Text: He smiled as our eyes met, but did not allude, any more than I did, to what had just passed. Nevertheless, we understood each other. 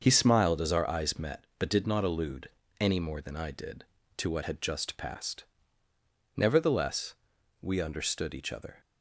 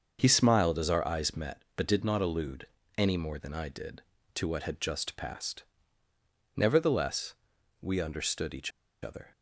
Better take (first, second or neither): first